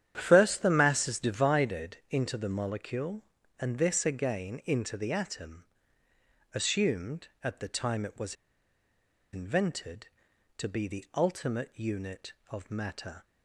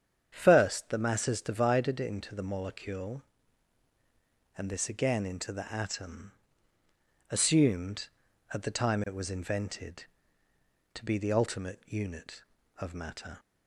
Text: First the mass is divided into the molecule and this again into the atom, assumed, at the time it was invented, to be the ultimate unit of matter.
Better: second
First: starts louder than the rest; strong; until 1.1 s; 9.5 dB // pauses between "was" and "invented"; at 8.3 s; 0.98 s long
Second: starts louder than the rest; strong; until 1.3 s; 8 dB

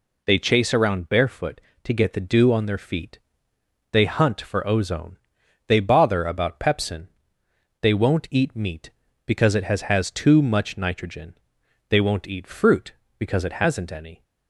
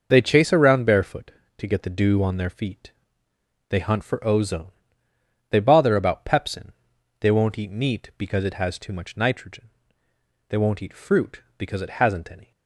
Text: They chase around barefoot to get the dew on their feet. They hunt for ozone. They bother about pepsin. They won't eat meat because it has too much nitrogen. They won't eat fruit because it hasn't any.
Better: second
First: says "has" twice; at 9.8 s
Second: none

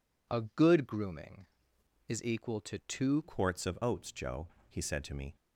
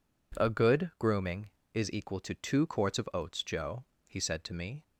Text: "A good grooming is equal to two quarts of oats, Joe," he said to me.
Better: second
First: changes voice at "quarts"; from 3.2 s on; 2.1 s long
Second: none

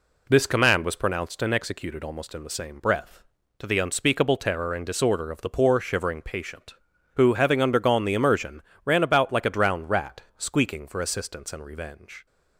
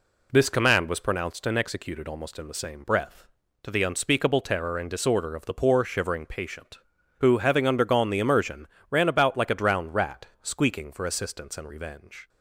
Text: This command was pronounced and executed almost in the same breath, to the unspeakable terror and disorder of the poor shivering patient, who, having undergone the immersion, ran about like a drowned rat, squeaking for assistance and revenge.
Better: neither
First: none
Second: none

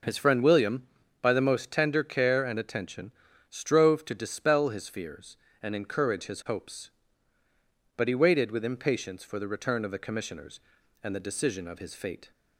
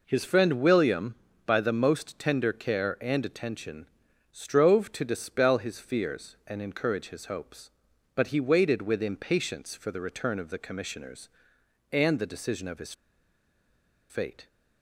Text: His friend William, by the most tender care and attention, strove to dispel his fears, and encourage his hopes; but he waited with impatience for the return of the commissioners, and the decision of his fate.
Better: first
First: none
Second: pauses between "his" and "fate"; at 12.9 s; 1.1 s long

